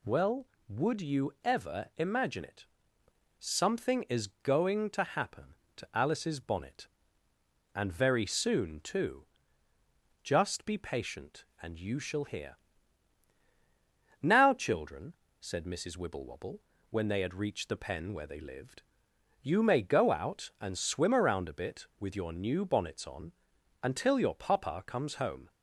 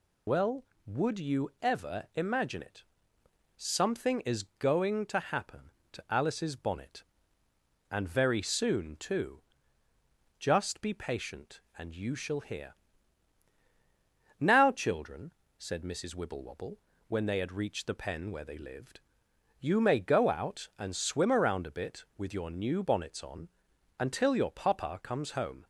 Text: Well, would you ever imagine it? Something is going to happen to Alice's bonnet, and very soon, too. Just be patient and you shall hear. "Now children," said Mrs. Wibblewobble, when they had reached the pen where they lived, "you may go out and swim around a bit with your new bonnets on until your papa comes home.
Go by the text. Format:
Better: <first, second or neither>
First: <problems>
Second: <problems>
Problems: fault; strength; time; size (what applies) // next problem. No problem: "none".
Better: first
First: pauses between "on" and "until"; noticeable; at 23.3 s; 0.50 s long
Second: loses the start of "Well"; at 0.2 s; 50 ms // pauses between "on" and "until"; noticeable; at 23.4 s; 0.50 s long